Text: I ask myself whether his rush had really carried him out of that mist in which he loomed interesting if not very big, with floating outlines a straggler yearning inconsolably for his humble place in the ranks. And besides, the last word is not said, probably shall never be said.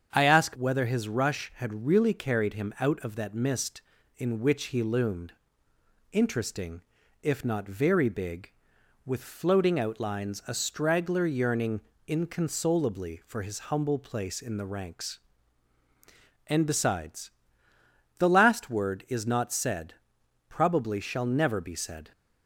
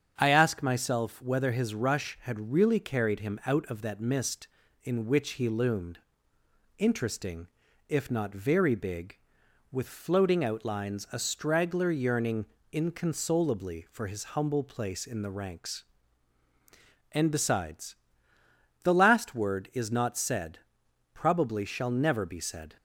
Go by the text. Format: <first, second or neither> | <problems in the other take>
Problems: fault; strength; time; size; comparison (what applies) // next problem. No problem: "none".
second | starts louder than the rest; strong; until 1.1 s; 7.5 dB; strong in the second // skips "myself"; at 0.5 s // pauses between "loomed" and "interesting"; noticeable; at 5.3 s; 0.78 s long; noticeable in the second // pauses between "interesting" and "if"; at 6.8 s; 0.40 s long; also in the second // pauses between "yearning" and "inconsolably"; slight; at 11.8 s; 0.24 s long; slight in the second